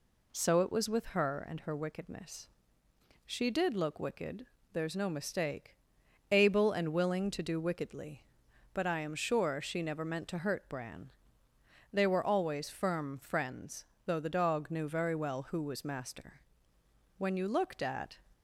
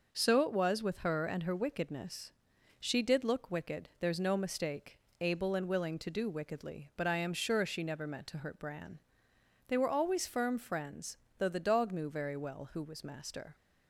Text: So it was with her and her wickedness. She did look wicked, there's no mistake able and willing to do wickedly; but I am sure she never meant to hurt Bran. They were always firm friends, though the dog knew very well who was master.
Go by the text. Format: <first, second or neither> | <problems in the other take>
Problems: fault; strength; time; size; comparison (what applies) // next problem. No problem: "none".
second | pauses between "mistake" and "able"; noticeable; at 5.7 s; 0.56 s long; slight in the second // goes on to say "When you looked at"; noticeable; from 17.1 s on; 1.0 s long